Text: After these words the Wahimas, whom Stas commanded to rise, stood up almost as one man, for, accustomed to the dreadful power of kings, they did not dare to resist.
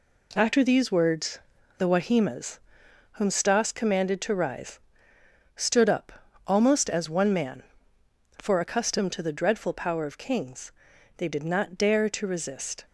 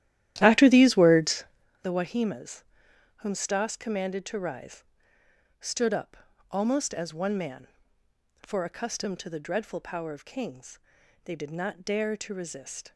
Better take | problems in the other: first | starts louder than the rest; strong; until 1.6 s; 13 dB // pauses between "words" and "the"; at 1.4 s; 0.37 s long; also in the first // pauses between "up" and "almost"; slight; at 6.1 s; 0.34 s long; slight in the first

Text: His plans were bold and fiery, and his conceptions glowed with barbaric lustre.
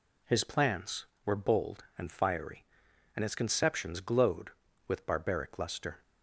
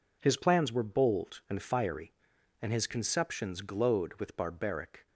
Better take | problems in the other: first | stops before "lustre"; at 5.0 s

